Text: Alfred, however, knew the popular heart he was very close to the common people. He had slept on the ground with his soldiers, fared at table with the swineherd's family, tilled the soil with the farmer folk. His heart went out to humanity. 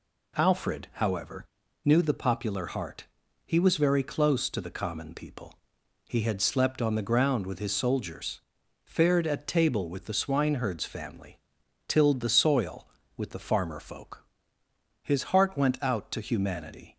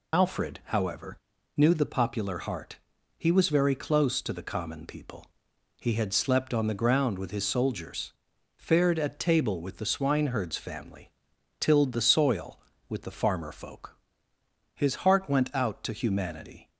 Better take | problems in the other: first | loses the start of "Alfred"; at 0.1 s; 75 ms // pauses between "heart" and "he"; at 2.7 s; 0.42 s long; also in the first

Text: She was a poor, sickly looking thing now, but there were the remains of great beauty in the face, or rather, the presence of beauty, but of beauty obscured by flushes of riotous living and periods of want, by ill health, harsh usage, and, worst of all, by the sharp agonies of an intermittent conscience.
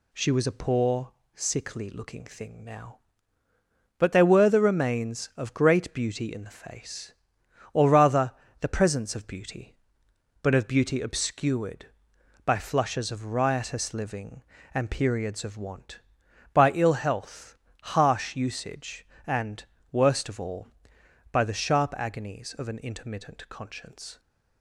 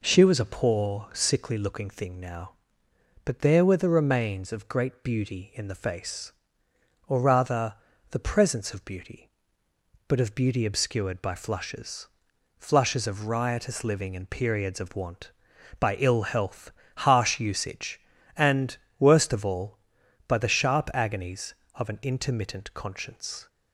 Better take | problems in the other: first | says "flushes" twice; at 12.5 s

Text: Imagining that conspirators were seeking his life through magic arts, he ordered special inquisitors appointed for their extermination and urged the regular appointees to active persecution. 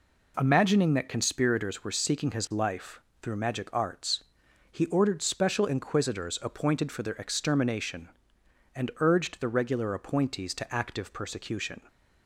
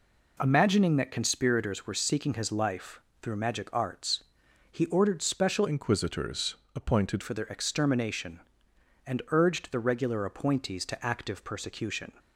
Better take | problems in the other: first | pauses between "life" and "through"; slight; at 3.0 s; 0.22 s long; slight in the first // changes voice from "inquisitors" to "appointed"; from 5.6 to 7.2 s; 1.6 s long // pauses between "inquisitors" and "appointed"; slight; at 6.5 s; 0.20 s long

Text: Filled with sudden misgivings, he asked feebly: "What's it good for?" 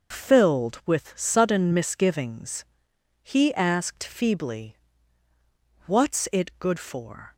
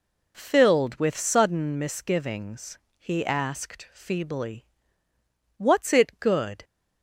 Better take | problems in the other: first | stops before "for"; at 6.6 s

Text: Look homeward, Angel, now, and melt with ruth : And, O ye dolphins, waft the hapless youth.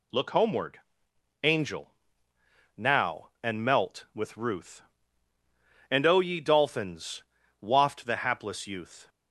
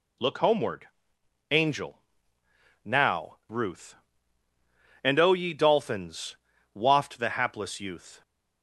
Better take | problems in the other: first | skips "and melt with"; at 3.4 s

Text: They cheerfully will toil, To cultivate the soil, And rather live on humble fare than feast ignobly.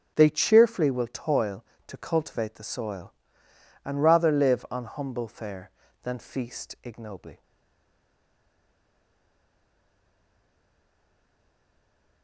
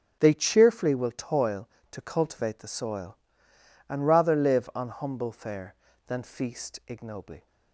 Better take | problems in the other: second | starts louder than the rest; until 1.1 s; 6.5 dB; strong in the second // stays silent after the last word; strong; from 7.4 s on; 4.8 s long

